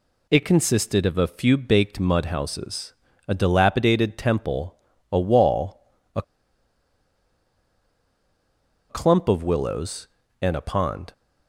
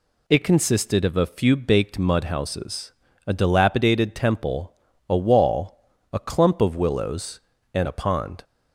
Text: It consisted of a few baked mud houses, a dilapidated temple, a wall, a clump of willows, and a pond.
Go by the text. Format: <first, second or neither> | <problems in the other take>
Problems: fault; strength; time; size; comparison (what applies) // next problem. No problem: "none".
second | pauses between "a" and "clump"; strong; at 6.2 s; 2.6 s long